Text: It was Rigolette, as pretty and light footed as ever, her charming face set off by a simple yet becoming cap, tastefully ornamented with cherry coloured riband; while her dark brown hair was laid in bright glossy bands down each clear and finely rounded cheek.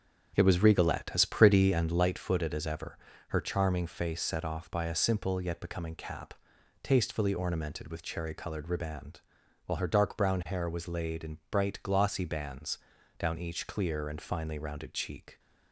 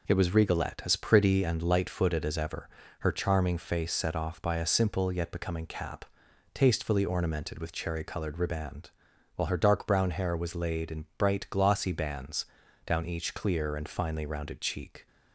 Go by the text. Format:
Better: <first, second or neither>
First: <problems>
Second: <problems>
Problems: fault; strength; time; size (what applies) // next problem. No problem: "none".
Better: second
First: starts louder than the rest; strong; until 2.1 s; 7.5 dB // pauses between "bands" and "down"; at 12.7 s; 0.40 s long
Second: pauses between "bands" and "down"; at 12.4 s; 0.40 s long